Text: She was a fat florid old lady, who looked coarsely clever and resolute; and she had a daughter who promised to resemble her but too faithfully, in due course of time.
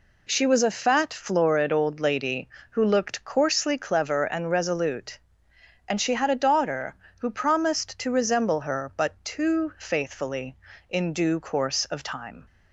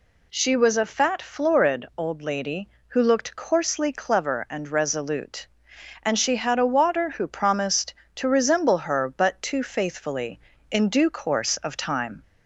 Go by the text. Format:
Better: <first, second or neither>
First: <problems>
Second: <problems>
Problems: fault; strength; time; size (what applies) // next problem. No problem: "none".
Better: first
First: none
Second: says "water" for "daughter"; at 6.6 s